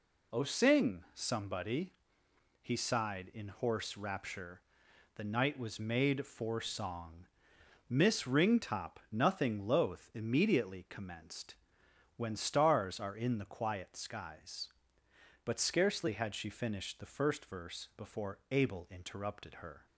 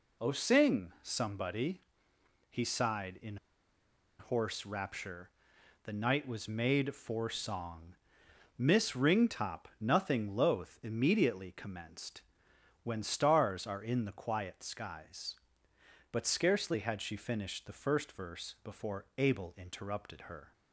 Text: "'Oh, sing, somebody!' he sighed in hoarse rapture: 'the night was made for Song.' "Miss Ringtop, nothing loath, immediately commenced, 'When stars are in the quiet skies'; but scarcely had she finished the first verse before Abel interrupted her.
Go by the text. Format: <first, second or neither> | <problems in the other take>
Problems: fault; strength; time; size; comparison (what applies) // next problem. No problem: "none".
first | pauses between "in" and "hoarse"; noticeable; at 3.3 s; 0.82 s long